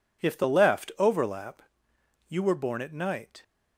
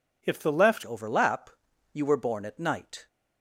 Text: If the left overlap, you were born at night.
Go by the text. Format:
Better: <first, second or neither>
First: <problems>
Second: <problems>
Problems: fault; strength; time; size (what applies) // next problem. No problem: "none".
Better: first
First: none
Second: changes voice at "overlap"; from 0.8 s on; 2.2 s long